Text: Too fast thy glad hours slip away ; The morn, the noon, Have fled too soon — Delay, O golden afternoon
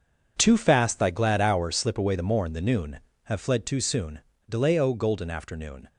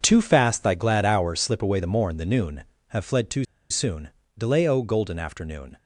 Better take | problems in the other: first | pauses between "too" and "soon"; slight; at 3.4 s; 0.26 s long

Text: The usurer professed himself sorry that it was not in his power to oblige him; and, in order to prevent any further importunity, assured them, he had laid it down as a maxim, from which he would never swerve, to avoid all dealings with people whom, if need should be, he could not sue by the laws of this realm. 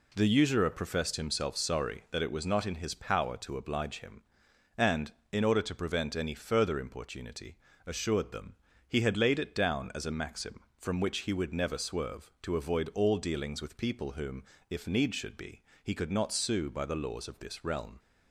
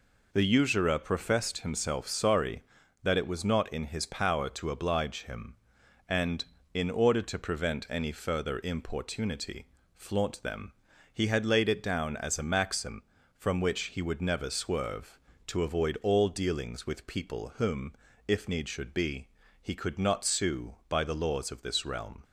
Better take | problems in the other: first | says "flaunt" for "assured"; at 9.9 s

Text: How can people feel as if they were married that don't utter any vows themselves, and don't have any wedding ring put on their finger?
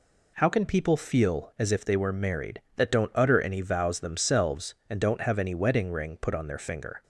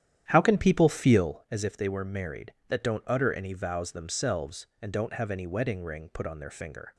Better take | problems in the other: first | starts louder than the rest; strong; until 1.3 s; 10.5 dB

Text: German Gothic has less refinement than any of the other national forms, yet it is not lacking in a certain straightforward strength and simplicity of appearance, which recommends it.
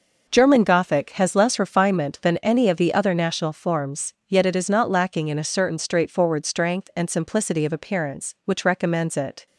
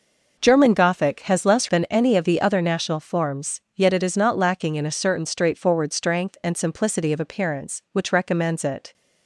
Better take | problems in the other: first | skips "refinement"; at 1.6 s

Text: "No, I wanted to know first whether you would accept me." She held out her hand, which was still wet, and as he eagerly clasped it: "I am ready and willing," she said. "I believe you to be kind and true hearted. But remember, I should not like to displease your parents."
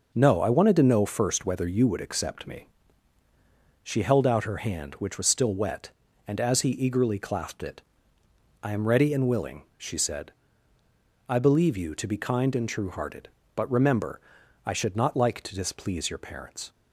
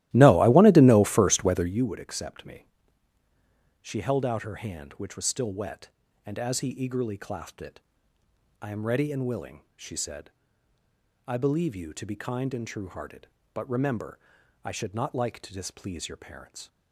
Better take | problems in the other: first | starts louder than the rest; strong; until 1.8 s; 15 dB

